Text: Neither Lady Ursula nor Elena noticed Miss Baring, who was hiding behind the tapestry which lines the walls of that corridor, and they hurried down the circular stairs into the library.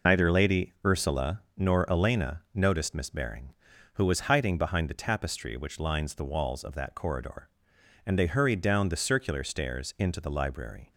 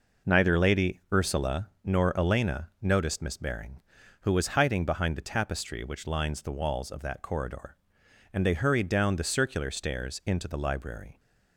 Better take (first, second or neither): second